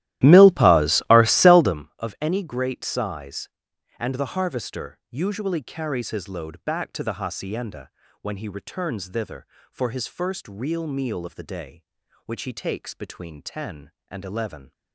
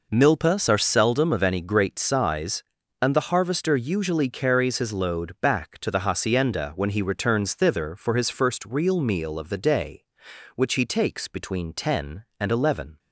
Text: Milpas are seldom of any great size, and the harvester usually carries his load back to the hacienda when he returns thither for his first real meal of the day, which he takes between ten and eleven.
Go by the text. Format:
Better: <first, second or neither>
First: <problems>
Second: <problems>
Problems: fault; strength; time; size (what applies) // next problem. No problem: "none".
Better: second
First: starts louder than the rest; strong; until 1.8 s; 14.5 dB // pauses between "hacienda" and "when"; slight; at 7.8 s; 0.32 s long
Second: none